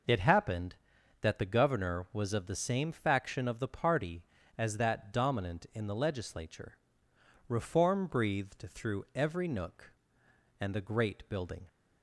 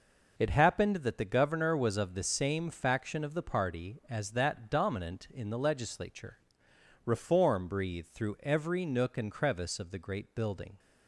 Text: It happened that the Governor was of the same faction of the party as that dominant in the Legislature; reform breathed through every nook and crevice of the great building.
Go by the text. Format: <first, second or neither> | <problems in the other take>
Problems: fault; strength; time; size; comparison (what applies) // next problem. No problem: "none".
second | skips "crevice of"; at 10.7 s